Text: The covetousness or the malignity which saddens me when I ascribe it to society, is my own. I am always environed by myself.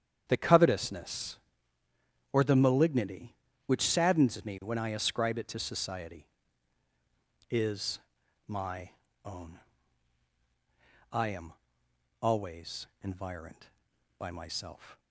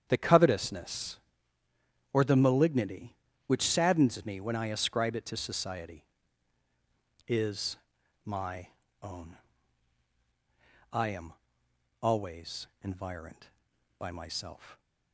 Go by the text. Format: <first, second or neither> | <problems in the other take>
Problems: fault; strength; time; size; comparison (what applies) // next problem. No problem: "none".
neither | starts louder than the rest; strong; the same in both // pauses between "is" and "my"; noticeable; the same in both // pauses between "my" and "own"; slight; the same in both // pauses between "am" and "always"; noticeable; the same in both // pauses between "always" and "environed"; slight; the same in both